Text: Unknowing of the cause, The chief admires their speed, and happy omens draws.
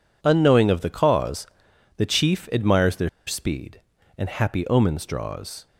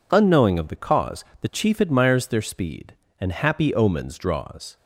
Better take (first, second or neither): second